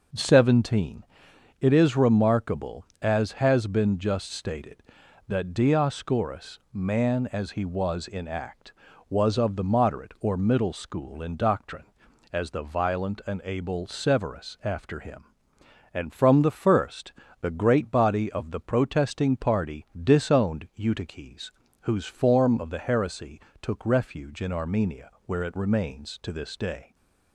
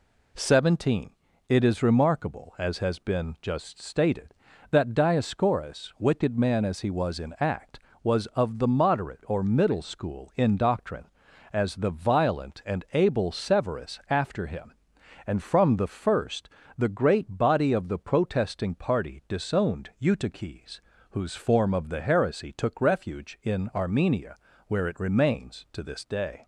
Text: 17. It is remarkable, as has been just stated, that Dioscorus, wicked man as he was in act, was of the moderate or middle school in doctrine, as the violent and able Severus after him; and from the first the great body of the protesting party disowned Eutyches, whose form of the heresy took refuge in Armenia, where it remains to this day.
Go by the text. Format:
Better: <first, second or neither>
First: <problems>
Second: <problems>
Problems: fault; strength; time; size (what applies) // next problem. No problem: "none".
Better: second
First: skips "wicked"; at 6.6 s // pauses between "first" and "the"; slight; at 17.1 s; 0.28 s long // pauses between "heresy" and "took"; slight; at 23.3 s; 0.22 s long // stays silent after the last word; slight; from 26.8 s on; 0.5 s long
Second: pauses between "first" and "the"; slight; at 16.4 s; 0.28 s long